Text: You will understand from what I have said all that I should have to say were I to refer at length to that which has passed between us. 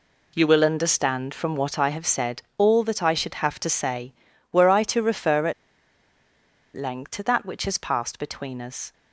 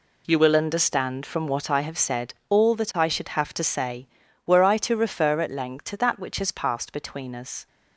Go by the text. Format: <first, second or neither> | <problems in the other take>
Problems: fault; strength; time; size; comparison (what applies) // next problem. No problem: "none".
second | pauses between "said" and "all"; slight; at 2.4 s; 0.16 s long; slight in the second // pauses between "at" and "length"; at 5.5 s; 1.2 s long